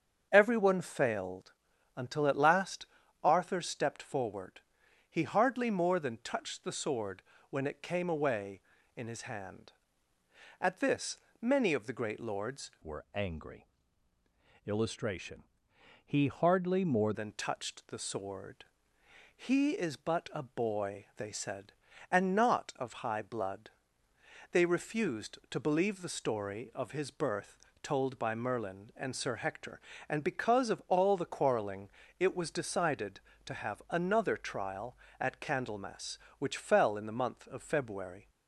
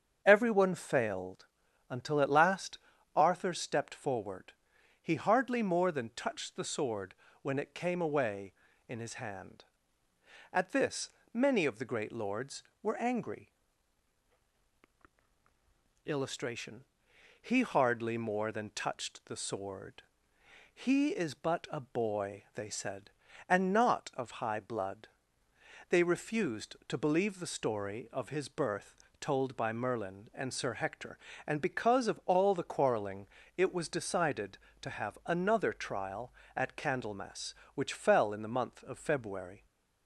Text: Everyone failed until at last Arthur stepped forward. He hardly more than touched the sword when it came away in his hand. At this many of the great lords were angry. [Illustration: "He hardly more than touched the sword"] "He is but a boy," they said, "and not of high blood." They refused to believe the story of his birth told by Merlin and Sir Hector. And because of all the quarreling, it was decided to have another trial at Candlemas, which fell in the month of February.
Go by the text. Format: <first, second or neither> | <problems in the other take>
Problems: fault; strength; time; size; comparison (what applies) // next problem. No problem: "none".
second | starts louder than the rest; strong; until 1.3 s; 7.5 dB; strong in the second // pauses between "failed" and "until"; at 1.5 s; 0.42 s long; also in the second // pauses between "last" and "Arthur"; slight; at 2.8 s; 0.36 s long; slight in the second // pauses between "sword" and "when"; slight; at 7.2 s; 0.28 s long; slight in the second // pauses between "this" and "many"; slight; at 11.1 s; 0.24 s long; slight in the second // changes voice from "were" to "more"; from 12.8 to 17.1 s; 4.3 s long // pauses between "sword" and "He"; noticeable; at 18.6 s; 0.70 s long; noticeable in the second // pauses between "birth" and "told"; slight; at 27.5 s; 0.24 s long; slight in the second